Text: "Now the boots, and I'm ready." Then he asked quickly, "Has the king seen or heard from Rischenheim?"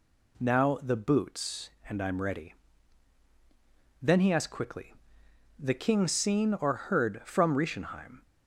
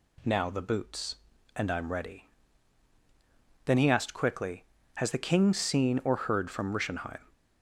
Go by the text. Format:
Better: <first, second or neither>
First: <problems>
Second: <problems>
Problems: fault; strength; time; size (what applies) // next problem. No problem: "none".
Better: second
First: skips "Has"; at 5.2 s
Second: none